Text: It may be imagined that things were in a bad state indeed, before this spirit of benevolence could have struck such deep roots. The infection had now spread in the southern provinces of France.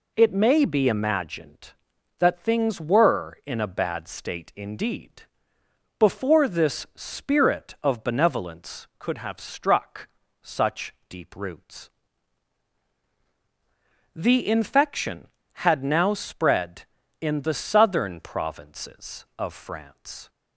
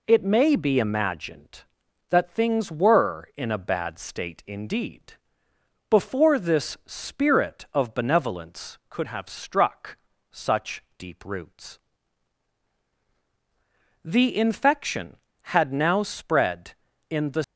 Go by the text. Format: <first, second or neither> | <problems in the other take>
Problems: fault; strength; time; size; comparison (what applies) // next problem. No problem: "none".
first | pauses between "struck" and "such"; slight; at 9.9 s; 0.36 s long; slight in the first // pauses between "such" and "deep"; slight; at 10.8 s; 0.16 s long; slight in the first // stops before "southern provinces of France"; at 17.4 s